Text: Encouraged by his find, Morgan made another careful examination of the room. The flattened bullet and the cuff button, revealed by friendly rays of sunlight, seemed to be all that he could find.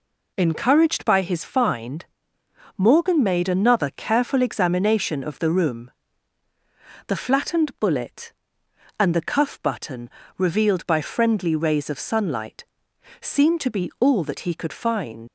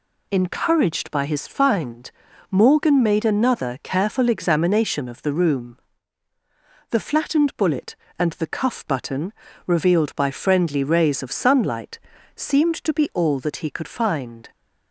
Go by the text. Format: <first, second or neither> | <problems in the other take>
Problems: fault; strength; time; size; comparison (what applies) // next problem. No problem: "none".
second | leaves "find" unfinished; at 15.2 s; 75 ms